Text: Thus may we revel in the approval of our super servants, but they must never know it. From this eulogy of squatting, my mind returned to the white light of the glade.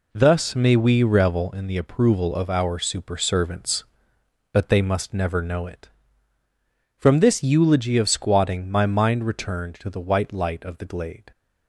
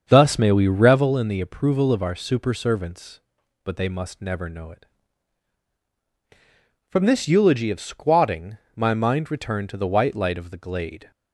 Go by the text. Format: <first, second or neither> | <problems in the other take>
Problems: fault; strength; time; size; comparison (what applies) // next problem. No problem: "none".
first | starts louder than the rest; until 1.0 s; 7 dB